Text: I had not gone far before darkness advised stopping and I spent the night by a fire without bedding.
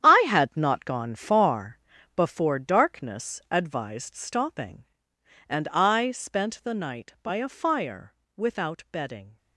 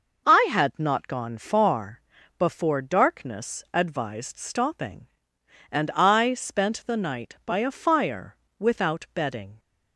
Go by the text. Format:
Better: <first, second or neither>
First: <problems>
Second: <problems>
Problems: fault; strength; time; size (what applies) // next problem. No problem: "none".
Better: second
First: gets quieter; strong; throughout; 11 dB // pauses between "far" and "before"; at 1.7 s; 0.38 s long // pauses between "fire" and "without"; slight; at 8.1 s; 0.20 s long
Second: pauses between "far" and "before"; at 2.0 s; 0.38 s long // pauses between "fire" and "without"; slight; at 8.3 s; 0.20 s long